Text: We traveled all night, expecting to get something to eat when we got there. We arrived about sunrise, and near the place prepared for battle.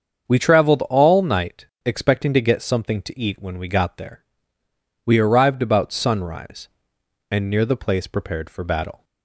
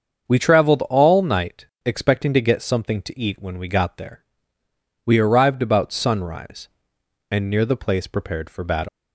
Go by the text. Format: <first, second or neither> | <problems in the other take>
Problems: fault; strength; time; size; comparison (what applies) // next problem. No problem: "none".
first | starts louder than the rest; until 1.3 s; 7 dB; also in the first // leaves "battle" unfinished; at 8.8 s; 150 ms